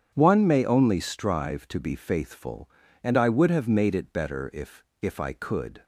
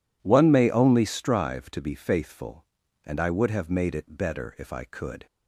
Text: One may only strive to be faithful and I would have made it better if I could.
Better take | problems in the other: second | starts louder than the rest; strong; until 1.1 s; 8.5 dB // says "if" twice; at 5.0 s

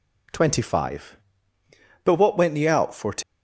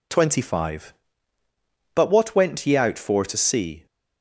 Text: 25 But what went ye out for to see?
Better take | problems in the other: second | stops before "see"; at 3.2 s

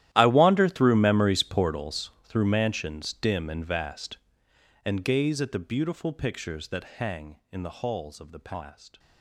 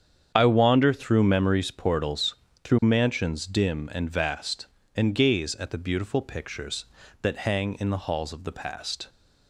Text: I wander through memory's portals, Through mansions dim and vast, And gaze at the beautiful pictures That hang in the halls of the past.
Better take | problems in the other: second | gets quieter; strong; throughout; 19.5 dB // starts louder than the rest; strong; until 1.1 s; 13 dB; strong in the second

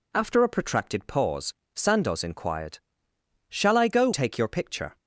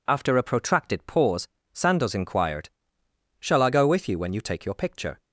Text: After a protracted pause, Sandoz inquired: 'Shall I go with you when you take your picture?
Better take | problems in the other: second | skips "with you when you"; at 4.1 s

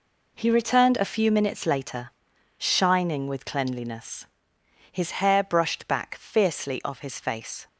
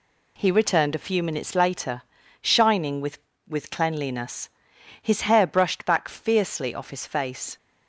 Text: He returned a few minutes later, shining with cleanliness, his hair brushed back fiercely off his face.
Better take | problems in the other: first | says "with" twice; at 3.4 s

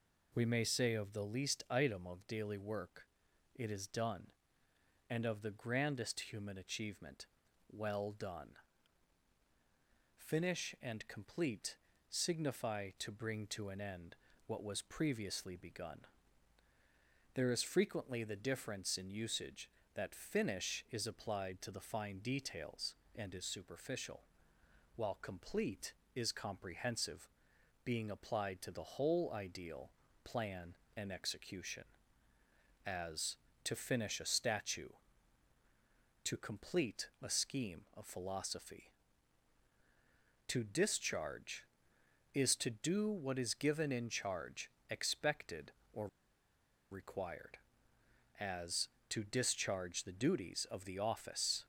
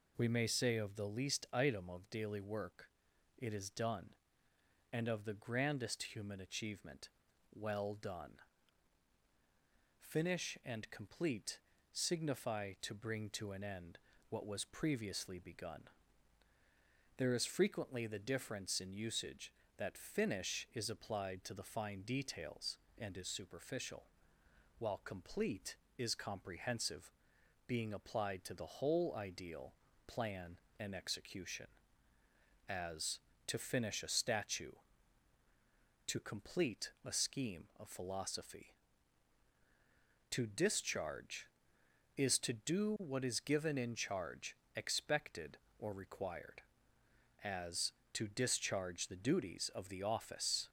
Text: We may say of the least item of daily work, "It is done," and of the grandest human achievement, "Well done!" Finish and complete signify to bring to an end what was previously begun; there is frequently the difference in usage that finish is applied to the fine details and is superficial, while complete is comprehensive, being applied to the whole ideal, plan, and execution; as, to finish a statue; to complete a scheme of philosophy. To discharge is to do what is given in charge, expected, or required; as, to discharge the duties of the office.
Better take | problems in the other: second | pauses between "complete" and "signify"; slight; at 11.7 s; 0.32 s long; slight in the second // pauses between "end" and "what"; slight; at 14.1 s; 0.32 s long; slight in the second // pauses between "or" and "required"; noticeable; at 46.0 s; 0.84 s long

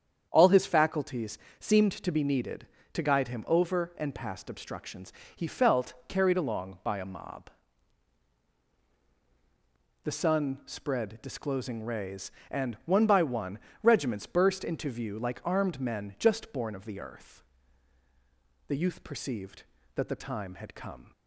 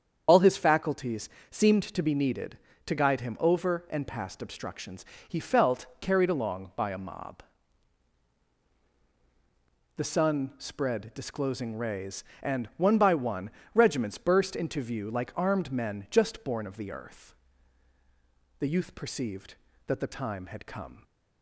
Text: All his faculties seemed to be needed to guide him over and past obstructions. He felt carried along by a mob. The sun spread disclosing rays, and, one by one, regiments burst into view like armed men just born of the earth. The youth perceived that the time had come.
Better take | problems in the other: first | loses the start of "All"; at 0.2 s; 65 ms // starts louder than the rest; strong; until 1.2 s; 7.5 dB; strong in the first // pauses between "faculties" and "seemed"; slight; at 1.2 s; 0.22 s long; slight in the first

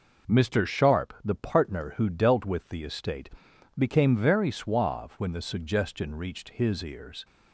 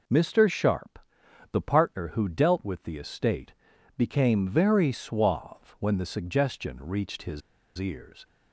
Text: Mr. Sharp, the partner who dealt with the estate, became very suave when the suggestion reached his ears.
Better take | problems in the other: first | pauses between "his" and "ears"; at 7.4 s; 0.37 s long

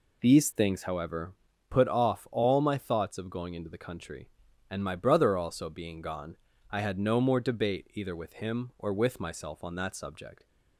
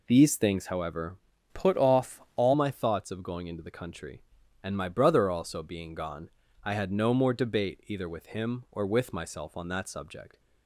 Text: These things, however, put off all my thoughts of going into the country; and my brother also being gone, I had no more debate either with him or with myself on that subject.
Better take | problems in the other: first | changes voice from "put" to "all"; from 1.5 to 2.5 s; 1.0 s long // pauses between "off" and "all"; slight; at 2.1 s; 0.20 s long

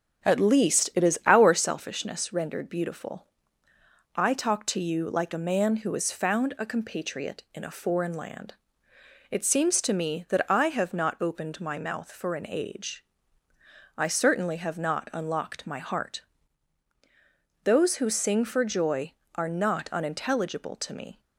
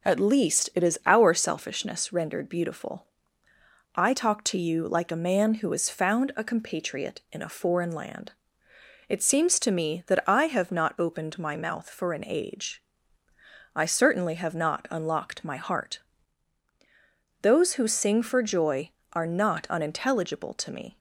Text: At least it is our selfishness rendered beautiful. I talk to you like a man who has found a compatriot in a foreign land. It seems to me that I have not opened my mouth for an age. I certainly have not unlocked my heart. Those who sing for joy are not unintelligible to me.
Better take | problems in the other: second | starts louder than the rest; strong; until 1.7 s; 7.5 dB

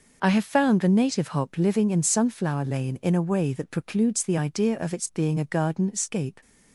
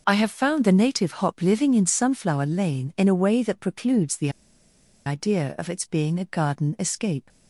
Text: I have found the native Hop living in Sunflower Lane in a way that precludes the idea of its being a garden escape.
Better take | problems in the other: first | pauses between "the" and "idea"; noticeable; at 4.2 s; 0.76 s long

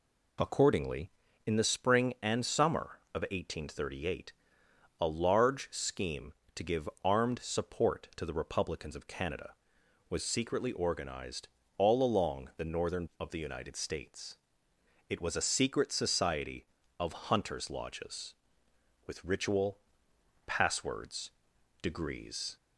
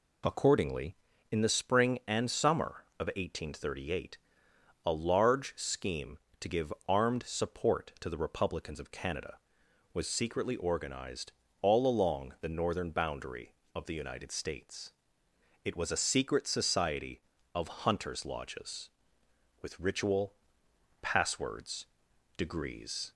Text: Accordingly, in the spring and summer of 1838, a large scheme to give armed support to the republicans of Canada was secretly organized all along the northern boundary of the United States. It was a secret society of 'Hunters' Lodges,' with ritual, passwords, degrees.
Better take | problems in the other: second | pauses between "give" and "armed"; slight; at 6.8 s; 0.16 s long; slight in the second // pauses between "organized" and "all"; slight; at 11.4 s; 0.28 s long; slight in the second // skips "boundary"; at 13.1 s

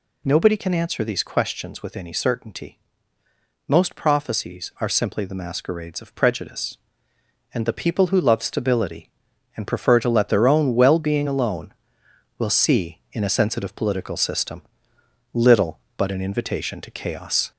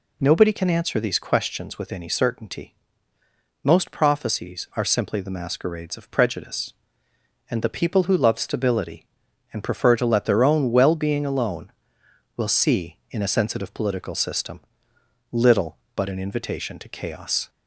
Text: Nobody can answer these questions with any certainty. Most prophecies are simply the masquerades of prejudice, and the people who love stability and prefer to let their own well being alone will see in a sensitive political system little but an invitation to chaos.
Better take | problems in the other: second | gets louder; slight; throughout; 2 dB // pauses between "system" and "little"; noticeable; at 14.6 s; 0.72 s long; noticeable in the second

